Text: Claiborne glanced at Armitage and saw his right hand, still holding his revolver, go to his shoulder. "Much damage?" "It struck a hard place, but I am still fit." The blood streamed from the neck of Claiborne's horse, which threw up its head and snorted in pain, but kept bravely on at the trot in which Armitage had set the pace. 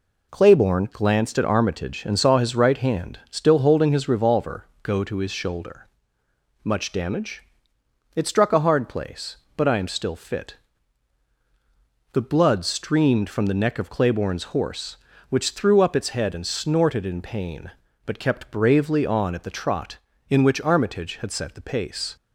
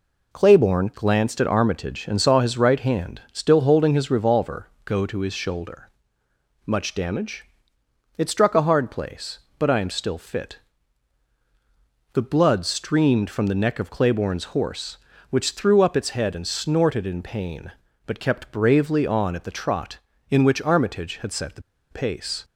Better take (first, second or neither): first